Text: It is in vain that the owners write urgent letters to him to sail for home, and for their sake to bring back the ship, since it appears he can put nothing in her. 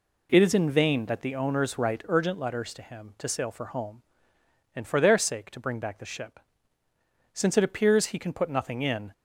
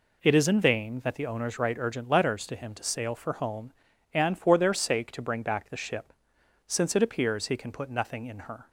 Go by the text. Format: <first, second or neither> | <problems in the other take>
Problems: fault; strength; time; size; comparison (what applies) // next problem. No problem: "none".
second | stops before "her"; at 9.1 s